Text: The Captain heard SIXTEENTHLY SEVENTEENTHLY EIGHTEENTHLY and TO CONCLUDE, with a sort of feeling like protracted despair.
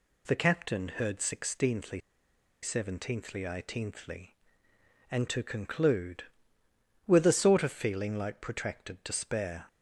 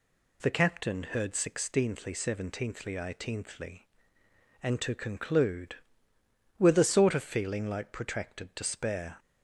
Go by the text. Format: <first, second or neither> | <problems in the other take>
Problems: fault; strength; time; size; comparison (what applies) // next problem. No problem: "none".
second | pauses between "SIXTEENTHLY" and "SEVENTEENTHLY"; noticeable; at 2.0 s; 0.62 s long